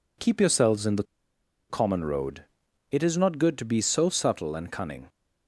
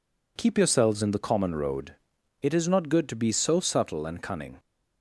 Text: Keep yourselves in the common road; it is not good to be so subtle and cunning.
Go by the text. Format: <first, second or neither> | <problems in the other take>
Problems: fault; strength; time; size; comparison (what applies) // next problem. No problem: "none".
second | pauses between "the" and "common"; noticeable; at 1.0 s; 0.66 s long